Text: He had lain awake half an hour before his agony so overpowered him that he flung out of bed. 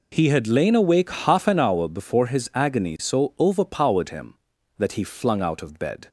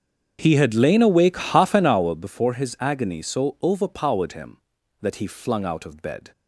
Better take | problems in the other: first | starts louder than the rest; strong; until 2.3 s; 7.5 dB

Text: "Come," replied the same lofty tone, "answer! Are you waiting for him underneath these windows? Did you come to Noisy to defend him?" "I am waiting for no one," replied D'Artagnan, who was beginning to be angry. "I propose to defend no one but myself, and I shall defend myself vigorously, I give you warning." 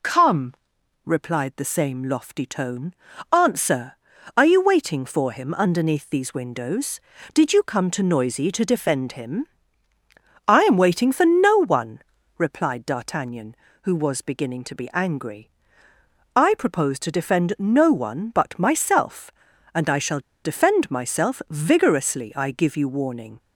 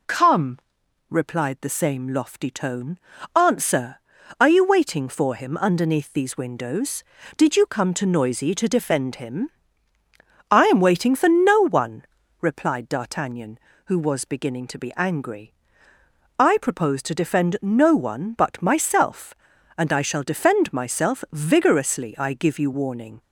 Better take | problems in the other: second | pauses between "shall" and "defend"; slight; at 20.2 s; 0.23 s long

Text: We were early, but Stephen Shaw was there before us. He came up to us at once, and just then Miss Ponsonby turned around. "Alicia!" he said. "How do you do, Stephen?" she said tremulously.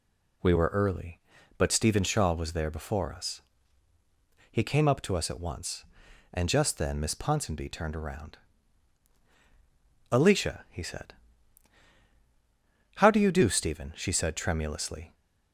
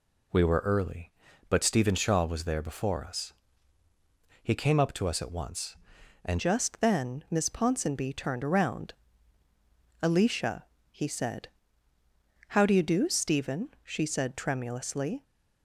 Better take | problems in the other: first | changes voice at "just"; from 6.3 s on; 8.9 s long

